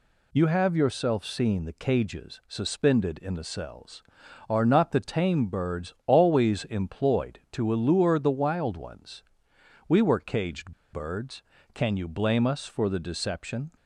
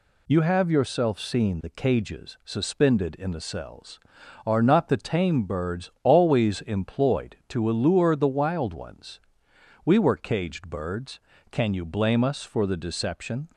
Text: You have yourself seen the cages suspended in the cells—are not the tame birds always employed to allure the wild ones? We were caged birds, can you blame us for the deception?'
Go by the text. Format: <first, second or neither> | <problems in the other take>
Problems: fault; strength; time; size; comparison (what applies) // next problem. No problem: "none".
second | pauses between "caged" and "birds"; slight; at 10.7 s; 0.20 s long